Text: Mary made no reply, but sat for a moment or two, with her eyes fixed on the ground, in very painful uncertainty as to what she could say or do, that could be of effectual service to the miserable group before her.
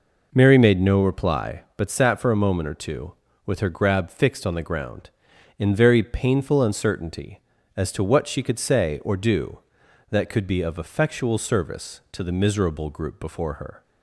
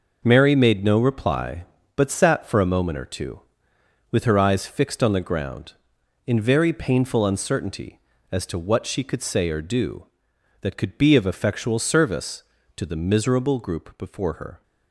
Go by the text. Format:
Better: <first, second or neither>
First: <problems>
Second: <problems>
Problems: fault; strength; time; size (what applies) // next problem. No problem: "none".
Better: second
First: says "grab" for "eyes"; at 3.6 s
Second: none